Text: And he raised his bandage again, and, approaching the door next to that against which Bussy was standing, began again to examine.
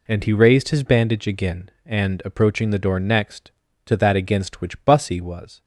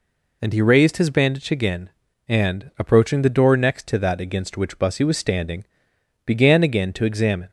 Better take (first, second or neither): second